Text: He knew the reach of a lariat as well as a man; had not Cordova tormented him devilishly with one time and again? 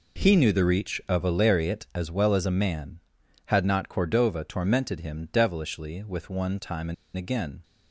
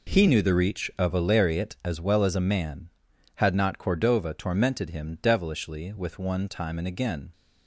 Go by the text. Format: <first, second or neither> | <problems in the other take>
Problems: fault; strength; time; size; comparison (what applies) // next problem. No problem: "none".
second | pauses between "and" and "again"; slight; at 6.9 s; 0.21 s long